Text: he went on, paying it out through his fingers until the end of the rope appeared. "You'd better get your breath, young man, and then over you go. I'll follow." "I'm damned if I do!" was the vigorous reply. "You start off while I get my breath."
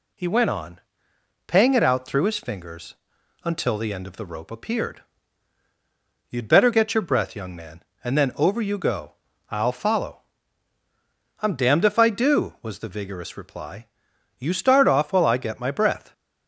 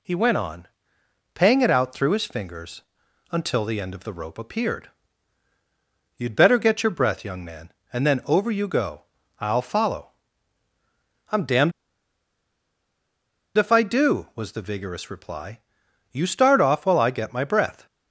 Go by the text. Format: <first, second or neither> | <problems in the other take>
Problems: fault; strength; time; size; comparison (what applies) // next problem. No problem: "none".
first | pauses between "fingers" and "until"; noticeable; at 2.8 s; 0.48 s long; noticeable in the first // pauses between "damned" and "if"; strong; at 11.7 s; 1.8 s long